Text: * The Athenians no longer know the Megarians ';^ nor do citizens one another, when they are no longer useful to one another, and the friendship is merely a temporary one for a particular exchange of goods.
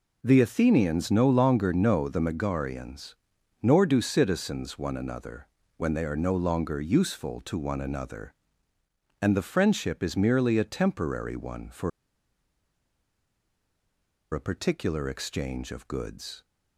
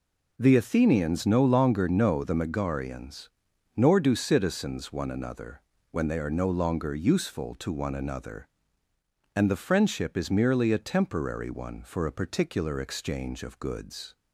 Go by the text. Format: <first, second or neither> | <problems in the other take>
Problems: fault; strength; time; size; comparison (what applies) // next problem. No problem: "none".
second | pauses between "for" and "a"; strong; at 11.9 s; 2.4 s long